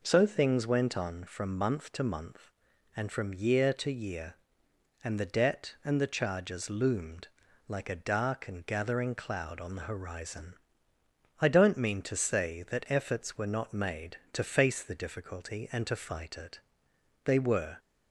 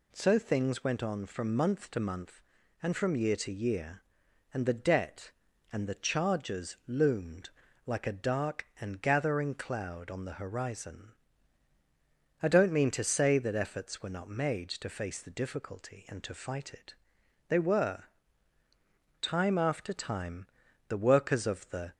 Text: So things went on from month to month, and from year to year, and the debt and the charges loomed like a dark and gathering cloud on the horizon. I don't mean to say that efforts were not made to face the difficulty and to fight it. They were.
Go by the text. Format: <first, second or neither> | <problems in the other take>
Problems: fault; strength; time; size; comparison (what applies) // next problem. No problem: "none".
first | pauses between "loomed" and "like"; slight; at 7.4 s; 0.36 s long; also in the first // goes on to say "Time after time the workers of the"; strong; from 19.2 s on; 2.7 s long